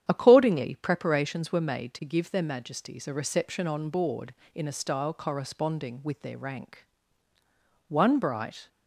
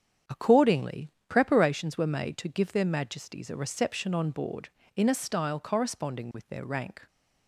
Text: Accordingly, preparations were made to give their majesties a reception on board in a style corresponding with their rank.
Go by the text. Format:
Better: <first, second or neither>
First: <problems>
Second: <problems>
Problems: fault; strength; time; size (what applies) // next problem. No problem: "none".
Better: second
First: starts louder than the rest; strong; until 1.0 s; 9.5 dB // goes on to say "One bright"; noticeable; from 7.8 s on; 0.80 s long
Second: starts louder than the rest; strong; until 1.4 s; 8 dB